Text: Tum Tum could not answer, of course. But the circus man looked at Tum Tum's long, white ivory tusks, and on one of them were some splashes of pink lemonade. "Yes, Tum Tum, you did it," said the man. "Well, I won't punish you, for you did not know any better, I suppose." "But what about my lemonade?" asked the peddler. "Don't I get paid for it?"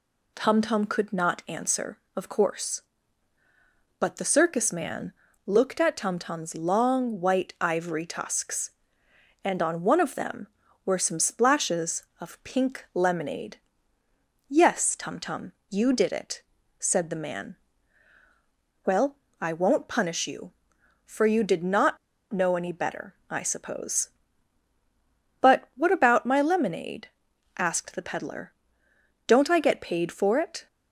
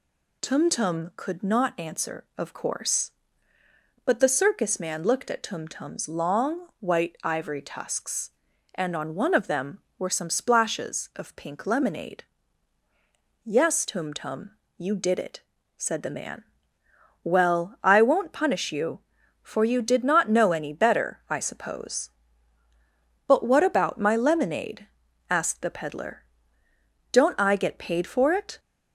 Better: second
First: pauses between "man" and "looked"; slight; at 5.1 s; 0.32 s long // pauses between "not" and "know"; slight; at 21.9 s; 0.35 s long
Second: none

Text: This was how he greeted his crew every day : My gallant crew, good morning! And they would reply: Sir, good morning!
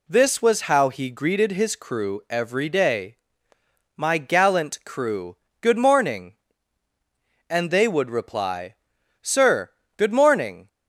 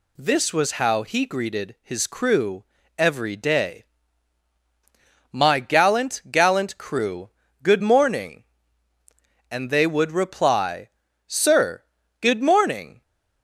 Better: first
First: none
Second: pauses between "crew" and "every"; slight; at 2.6 s; 0.32 s long // says "gallant" twice; at 6.3 s

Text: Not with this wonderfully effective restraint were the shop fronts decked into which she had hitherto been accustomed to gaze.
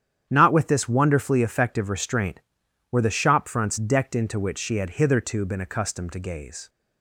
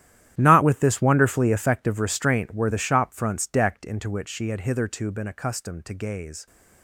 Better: first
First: starts louder than the rest; strong; until 1.3 s; 9.5 dB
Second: gets quieter; strong; throughout; 16.5 dB // starts louder than the rest; strong; until 1.3 s; 12 dB

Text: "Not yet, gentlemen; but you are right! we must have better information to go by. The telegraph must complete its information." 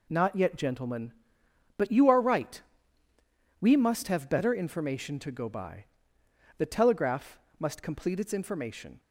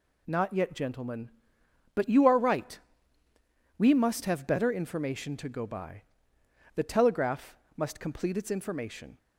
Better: second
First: starts louder than the rest; slight; until 1.2 s; 3 dB // pauses between "telegraph" and "must"; slight; at 7.3 s; 0.18 s long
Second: pauses between "telegraph" and "must"; slight; at 7.5 s; 0.18 s long

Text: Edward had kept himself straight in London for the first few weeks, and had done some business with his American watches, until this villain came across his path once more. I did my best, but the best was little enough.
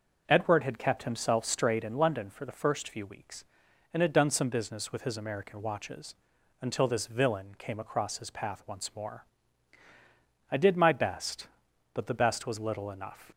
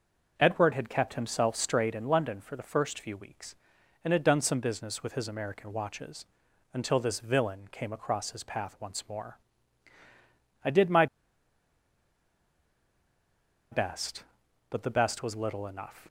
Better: first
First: none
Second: pauses between "my" and "best"; strong; at 11.0 s; 2.6 s long

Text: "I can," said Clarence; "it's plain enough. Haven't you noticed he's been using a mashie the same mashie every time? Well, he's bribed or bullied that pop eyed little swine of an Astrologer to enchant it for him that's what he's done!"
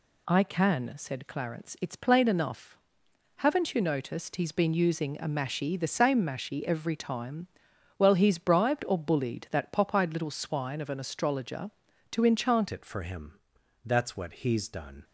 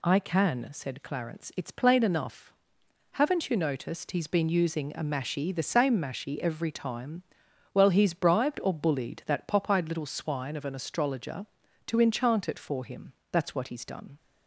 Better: second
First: changes voice at "it"; from 12.7 s on; 2.3 s long // pauses between "him" and "that's"; noticeable; at 13.3 s; 0.46 s long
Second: pauses between "him" and "that's"; slight; at 13.1 s; 0.18 s long

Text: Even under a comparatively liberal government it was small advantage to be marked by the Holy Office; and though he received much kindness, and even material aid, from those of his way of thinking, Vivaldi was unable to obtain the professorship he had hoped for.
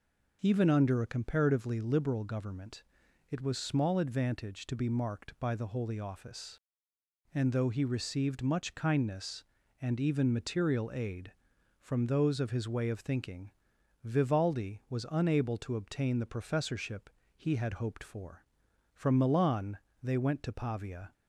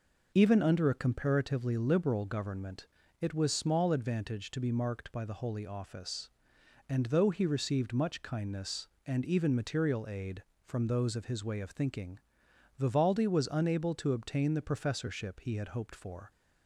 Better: second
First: pauses between "government" and "it"; noticeable; at 2.8 s; 0.48 s long // pauses between "professorship" and "he"; slight; at 17.0 s; 0.26 s long // goes on to say "From Milan they went to Pavia"; strong; from 18.9 s on; 2.2 s long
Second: pauses between "government" and "it"; slight; at 2.8 s; 0.34 s long

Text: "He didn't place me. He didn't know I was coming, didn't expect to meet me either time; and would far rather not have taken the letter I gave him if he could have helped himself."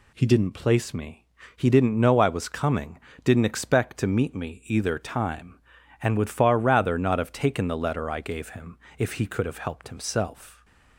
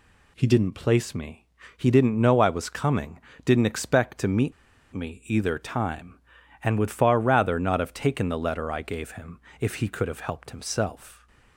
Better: first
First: pauses between "him" and "if"; slight; at 8.7 s; 0.22 s long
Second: pauses between "meet" and "me"; at 4.5 s; 0.42 s long // pauses between "him" and "if"; slight; at 9.3 s; 0.22 s long

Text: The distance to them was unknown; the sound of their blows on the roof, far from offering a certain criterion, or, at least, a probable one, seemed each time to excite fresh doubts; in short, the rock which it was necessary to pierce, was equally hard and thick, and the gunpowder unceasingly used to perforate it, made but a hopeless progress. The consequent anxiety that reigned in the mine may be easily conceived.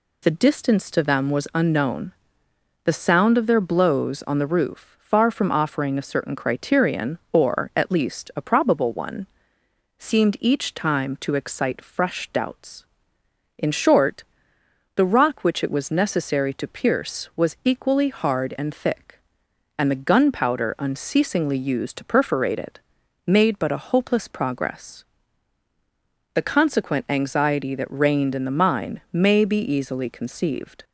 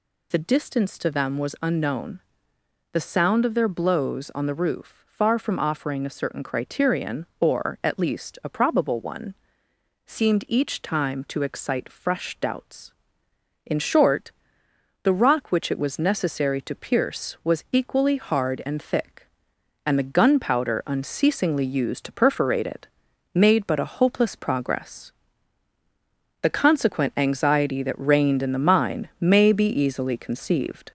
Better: first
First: none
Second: gets louder; slight; throughout; 3 dB

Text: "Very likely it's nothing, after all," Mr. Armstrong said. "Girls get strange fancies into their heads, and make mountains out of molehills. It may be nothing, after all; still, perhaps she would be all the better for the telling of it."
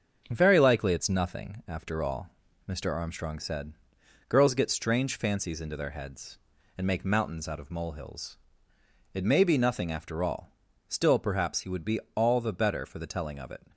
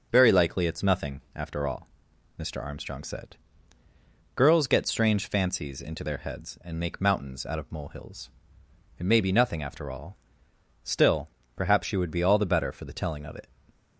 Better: second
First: starts louder than the rest; until 1.3 s; 6.5 dB // says "he" for "she"; at 11.6 s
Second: none

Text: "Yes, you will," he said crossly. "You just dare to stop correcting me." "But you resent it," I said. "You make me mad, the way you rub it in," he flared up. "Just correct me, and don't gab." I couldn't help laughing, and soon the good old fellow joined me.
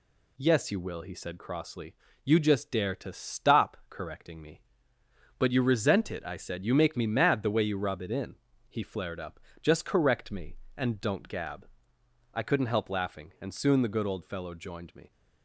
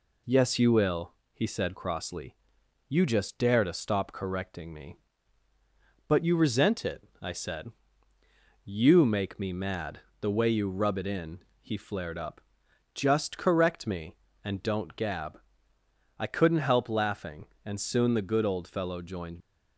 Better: first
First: none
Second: stops before "me"; at 19.4 s

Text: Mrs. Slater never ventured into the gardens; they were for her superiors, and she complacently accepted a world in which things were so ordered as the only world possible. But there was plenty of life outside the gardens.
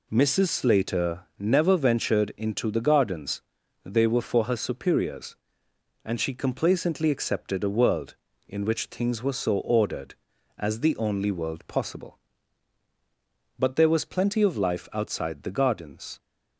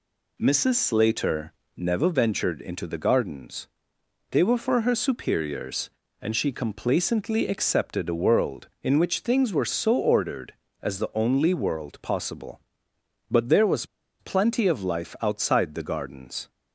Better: first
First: none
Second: pauses between "Slater" and "never"; slight; at 1.5 s; 0.22 s long // pauses between "was" and "plenty"; slight; at 13.8 s; 0.34 s long

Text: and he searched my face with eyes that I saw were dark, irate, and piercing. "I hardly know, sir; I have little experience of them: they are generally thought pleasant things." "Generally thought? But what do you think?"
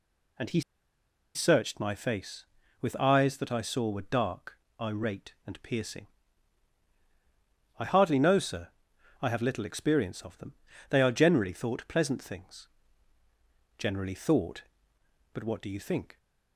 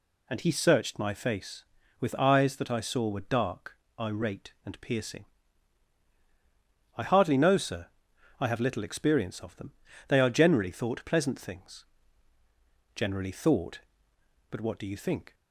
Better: second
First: pauses between "he" and "searched"; noticeable; at 0.6 s; 0.74 s long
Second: none

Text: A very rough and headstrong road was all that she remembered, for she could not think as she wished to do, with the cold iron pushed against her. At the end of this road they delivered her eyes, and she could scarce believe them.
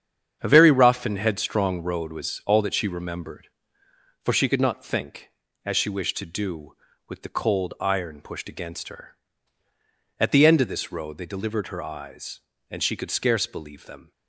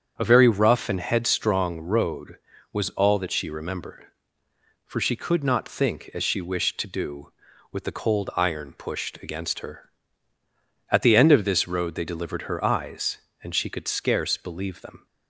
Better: neither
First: starts louder than the rest; strong; until 1.4 s; 8 dB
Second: starts louder than the rest; strong; until 1.1 s; 7.5 dB

